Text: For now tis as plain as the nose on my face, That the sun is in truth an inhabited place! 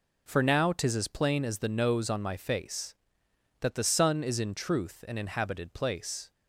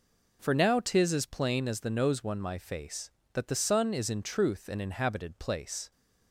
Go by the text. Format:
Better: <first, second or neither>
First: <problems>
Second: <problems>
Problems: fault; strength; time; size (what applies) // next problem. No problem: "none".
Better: first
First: none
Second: says "one" for "on"; at 2.2 s